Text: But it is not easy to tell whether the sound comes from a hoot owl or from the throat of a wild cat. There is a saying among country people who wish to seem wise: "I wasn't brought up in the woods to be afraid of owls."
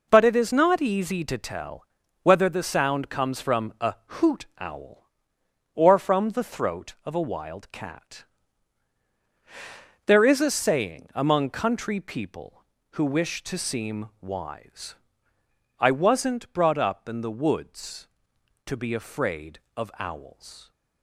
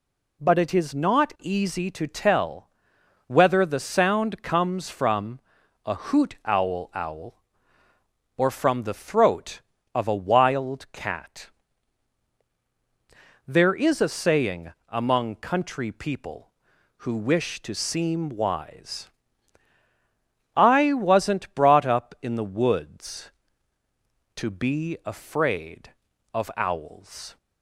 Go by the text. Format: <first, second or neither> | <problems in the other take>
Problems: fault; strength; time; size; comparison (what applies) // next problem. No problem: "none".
first | pauses between "tell" and "whether"; noticeable; at 2.6 s; 0.58 s long; also in the first // pauses between "from" and "a"; noticeable; at 5.3 s; 0.46 s long // says "owl" twice; at 6.9 s // pauses between "saying" and "among"; slight; at 14.7 s; 0.16 s long